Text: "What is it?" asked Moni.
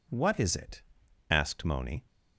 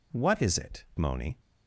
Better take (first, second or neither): first